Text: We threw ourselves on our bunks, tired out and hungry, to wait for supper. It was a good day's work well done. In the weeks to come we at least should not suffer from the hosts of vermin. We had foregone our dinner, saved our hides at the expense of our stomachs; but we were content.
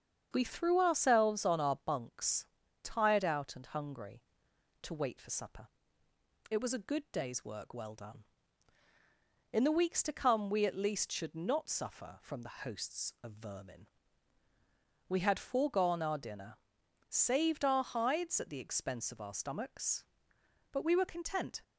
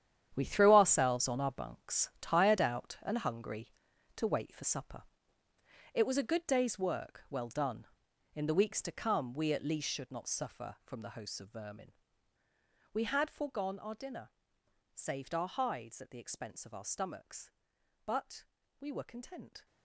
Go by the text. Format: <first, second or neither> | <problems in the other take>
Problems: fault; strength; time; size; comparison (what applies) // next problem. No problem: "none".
first | gets quieter; strong; throughout; 12.5 dB // starts louder than the rest; strong; until 1.3 s; 10 dB; strong in the first // pauses between "but" and "we"; slight; at 18.4 s; 0.34 s long